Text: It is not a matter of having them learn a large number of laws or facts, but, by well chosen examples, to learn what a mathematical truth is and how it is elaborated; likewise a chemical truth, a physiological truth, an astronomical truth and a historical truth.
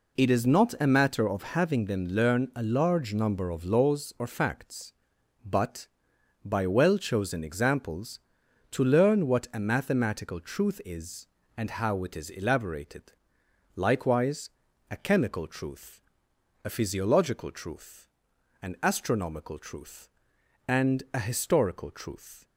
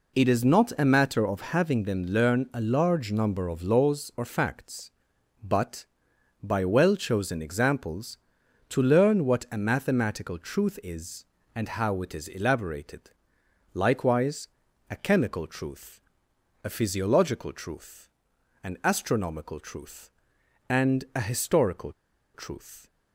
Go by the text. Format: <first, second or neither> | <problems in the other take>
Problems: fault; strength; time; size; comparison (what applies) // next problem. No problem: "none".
first | pauses between "likewise" and "a"; at 14.4 s; 0.38 s long; also in the first // pauses between "historical" and "truth"; at 21.9 s; 0.42 s long